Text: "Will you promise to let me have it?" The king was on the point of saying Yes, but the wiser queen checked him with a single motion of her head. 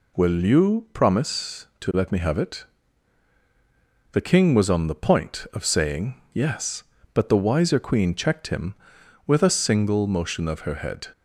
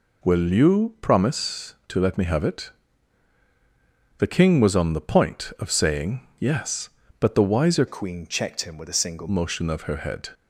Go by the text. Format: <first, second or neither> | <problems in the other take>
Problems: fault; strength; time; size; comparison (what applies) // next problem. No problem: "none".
first | changes voice from "queen" to "single"; from 7.8 to 9.2 s; 1.4 s long